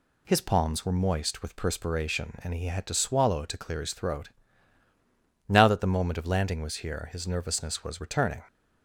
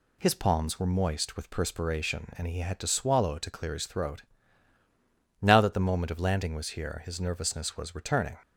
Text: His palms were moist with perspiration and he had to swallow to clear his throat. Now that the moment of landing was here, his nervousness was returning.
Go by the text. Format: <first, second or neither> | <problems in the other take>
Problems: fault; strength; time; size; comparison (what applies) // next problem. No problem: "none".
neither | none